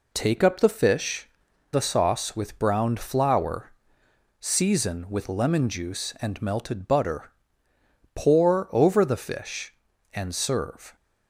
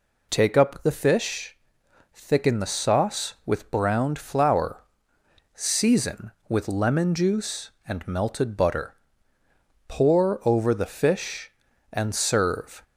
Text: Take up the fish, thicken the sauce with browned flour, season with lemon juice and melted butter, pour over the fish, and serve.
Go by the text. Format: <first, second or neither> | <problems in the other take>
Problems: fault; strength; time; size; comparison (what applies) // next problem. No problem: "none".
second | skips "thicken"; at 1.5 s